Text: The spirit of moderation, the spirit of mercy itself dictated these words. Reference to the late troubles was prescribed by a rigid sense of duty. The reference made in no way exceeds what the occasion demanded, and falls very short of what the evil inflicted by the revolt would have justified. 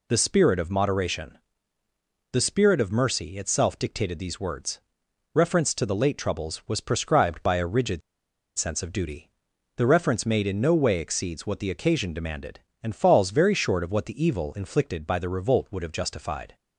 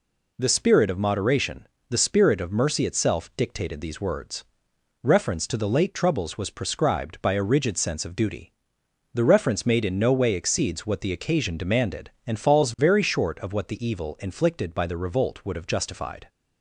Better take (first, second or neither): second